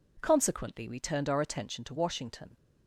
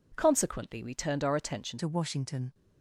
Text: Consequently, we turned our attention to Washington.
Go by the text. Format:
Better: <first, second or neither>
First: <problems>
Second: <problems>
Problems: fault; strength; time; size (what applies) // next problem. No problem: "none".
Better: first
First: none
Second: changes voice at "to"; from 1.7 s on; 0.8 s long